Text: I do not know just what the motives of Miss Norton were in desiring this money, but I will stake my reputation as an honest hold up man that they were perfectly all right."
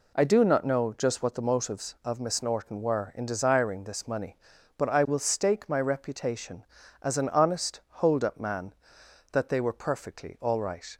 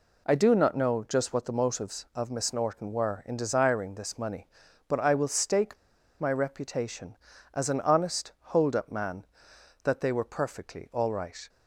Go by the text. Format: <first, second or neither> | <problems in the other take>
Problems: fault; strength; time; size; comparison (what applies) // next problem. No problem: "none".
first | pauses between "stake" and "my"; at 5.7 s; 0.43 s long